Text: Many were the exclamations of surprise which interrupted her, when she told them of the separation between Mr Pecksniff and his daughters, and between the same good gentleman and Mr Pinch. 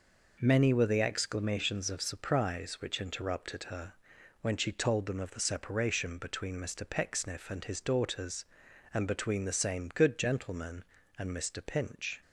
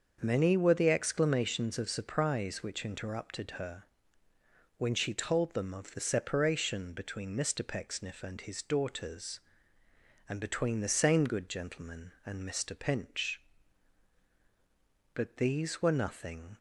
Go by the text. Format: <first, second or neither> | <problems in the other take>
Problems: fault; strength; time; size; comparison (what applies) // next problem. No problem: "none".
first | starts louder than the rest; until 1.2 s; 6.5 dB // goes on to say "But these were nothing"; from 15.1 s on; 1.4 s long